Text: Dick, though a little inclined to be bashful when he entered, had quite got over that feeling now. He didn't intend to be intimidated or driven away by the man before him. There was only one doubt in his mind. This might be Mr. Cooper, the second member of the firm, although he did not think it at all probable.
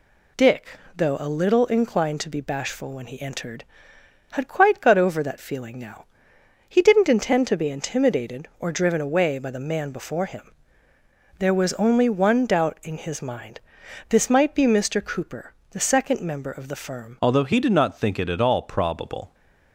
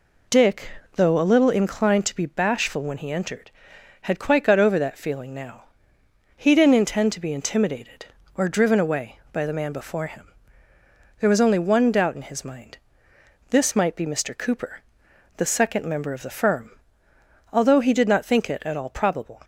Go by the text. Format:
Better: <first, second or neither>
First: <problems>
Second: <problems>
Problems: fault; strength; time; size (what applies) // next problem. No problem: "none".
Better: second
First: changes voice at "although"; from 17.2 s on; 2.1 s long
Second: none